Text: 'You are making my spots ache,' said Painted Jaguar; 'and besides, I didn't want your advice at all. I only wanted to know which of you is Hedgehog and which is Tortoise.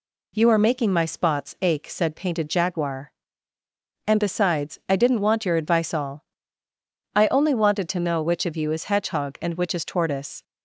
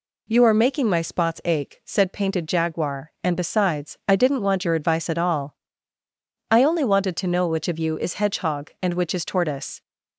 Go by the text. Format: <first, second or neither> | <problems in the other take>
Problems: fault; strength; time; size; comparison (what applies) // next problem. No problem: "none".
second | skips "at"; at 5.9 s